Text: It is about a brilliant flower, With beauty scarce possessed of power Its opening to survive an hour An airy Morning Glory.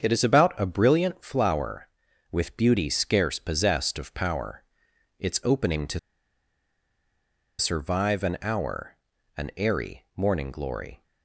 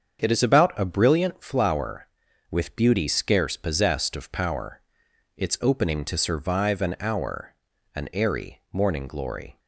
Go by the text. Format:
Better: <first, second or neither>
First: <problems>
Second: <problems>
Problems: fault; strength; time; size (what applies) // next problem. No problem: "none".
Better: second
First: starts louder than the rest; strong; until 1.0 s; 7 dB // pauses between "power" and "Its"; noticeable; at 4.6 s; 0.56 s long // pauses between "to" and "survive"; strong; at 5.9 s; 1.5 s long // pauses between "hour" and "An"; at 8.9 s; 0.40 s long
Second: starts louder than the rest; strong; until 1.2 s; 7 dB // pauses between "power" and "Its"; noticeable; at 4.8 s; 0.56 s long // pauses between "hour" and "An"; at 7.5 s; 0.40 s long